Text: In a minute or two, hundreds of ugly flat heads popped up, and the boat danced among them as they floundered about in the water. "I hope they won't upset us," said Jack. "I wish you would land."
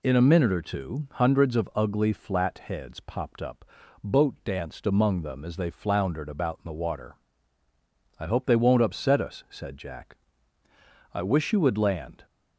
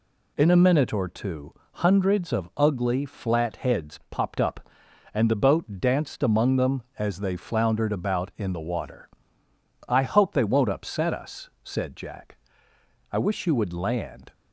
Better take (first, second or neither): second